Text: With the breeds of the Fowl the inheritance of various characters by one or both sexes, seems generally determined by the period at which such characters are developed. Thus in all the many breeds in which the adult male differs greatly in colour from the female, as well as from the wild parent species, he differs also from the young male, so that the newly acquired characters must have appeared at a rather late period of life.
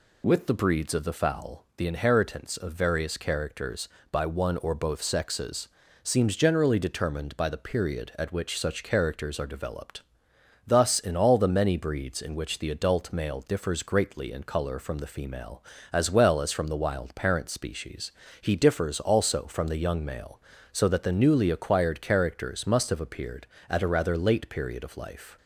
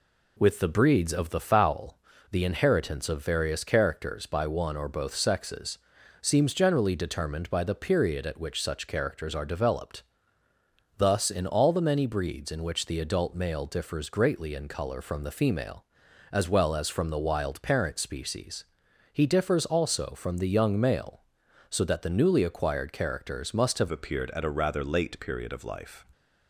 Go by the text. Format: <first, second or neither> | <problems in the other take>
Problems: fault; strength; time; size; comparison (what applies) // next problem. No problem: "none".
first | pauses between "Fowl" and "the"; slight; at 1.9 s; 0.32 s long // changes voice at "appeared"; from 23.9 s on; 2.1 s long